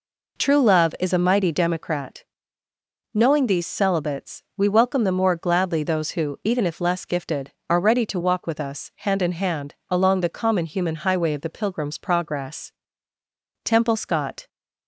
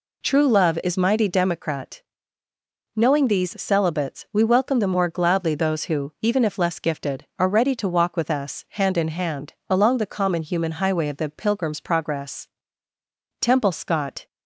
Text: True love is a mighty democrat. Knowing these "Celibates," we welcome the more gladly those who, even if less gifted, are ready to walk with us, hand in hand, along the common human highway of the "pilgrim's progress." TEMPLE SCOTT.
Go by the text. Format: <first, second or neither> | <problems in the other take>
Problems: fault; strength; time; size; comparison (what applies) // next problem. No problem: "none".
first | skips "a"; at 0.9 s